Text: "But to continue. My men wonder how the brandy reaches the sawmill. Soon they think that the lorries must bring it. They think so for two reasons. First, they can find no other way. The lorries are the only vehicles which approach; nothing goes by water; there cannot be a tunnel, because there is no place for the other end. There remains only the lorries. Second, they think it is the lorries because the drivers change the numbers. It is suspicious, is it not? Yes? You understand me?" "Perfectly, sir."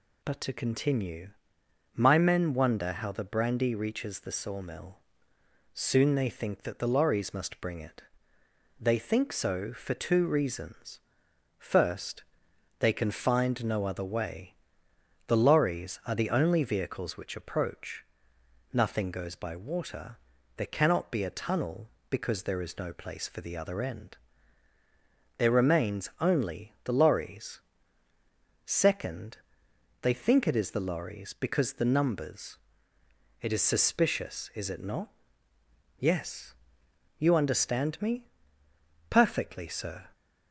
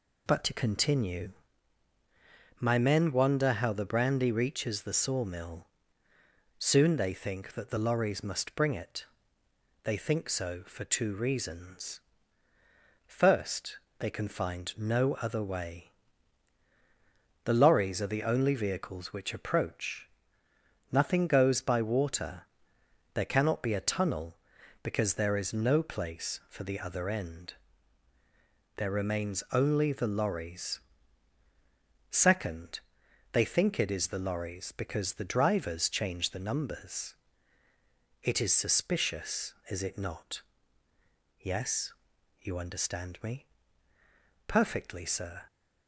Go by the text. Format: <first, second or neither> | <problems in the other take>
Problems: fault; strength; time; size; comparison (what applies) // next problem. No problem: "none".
second | skips "drivers change the"; at 31.8 s